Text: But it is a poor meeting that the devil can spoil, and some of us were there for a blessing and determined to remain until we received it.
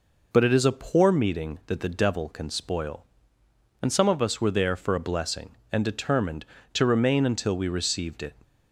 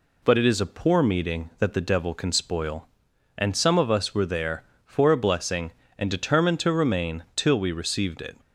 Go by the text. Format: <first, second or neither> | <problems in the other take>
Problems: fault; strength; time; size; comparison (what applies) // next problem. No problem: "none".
first | says "till" for "until"; at 7.3 s